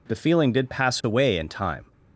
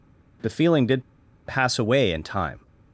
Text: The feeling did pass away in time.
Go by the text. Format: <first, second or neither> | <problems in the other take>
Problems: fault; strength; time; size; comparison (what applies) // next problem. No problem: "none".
first | pauses between "did" and "pass"; at 1.0 s; 0.45 s long